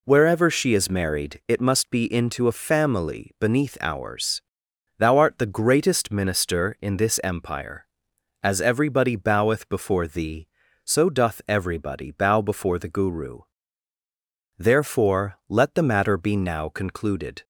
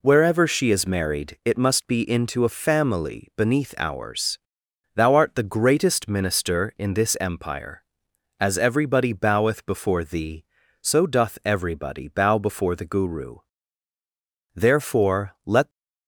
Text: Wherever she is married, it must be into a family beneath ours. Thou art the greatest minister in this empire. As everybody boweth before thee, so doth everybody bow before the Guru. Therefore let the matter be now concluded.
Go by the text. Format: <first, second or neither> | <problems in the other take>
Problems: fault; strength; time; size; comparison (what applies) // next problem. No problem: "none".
first | stops before "the matter be now concluded"; at 15.7 s